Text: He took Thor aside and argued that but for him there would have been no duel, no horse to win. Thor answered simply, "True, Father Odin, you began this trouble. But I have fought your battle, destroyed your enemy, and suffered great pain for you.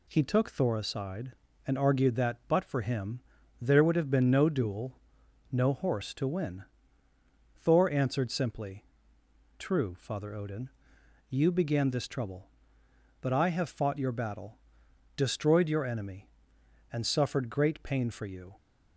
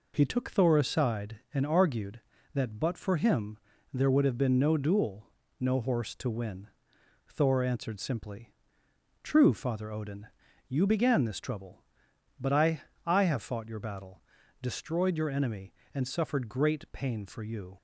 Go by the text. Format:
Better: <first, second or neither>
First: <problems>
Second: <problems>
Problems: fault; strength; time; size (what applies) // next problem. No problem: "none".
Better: first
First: pauses between "him" and "there"; at 3.1 s; 0.40 s long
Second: pauses between "him" and "there"; slight; at 3.5 s; 0.36 s long // says "I" twice; at 13.0 s